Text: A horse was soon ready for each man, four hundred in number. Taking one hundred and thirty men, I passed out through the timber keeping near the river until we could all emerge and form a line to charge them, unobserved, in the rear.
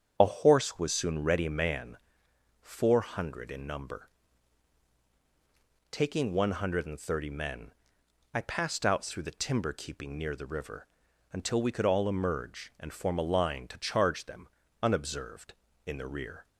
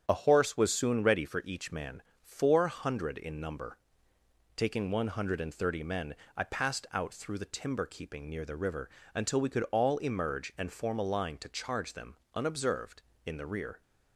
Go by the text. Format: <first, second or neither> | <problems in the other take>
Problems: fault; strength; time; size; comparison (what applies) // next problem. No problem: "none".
second | starts louder than the rest; strong; until 1.1 s; 8 dB; strong in the second // skips "for each"; at 1.4 s // pauses between "river" and "until"; at 10.8 s; 0.44 s long; slight in the second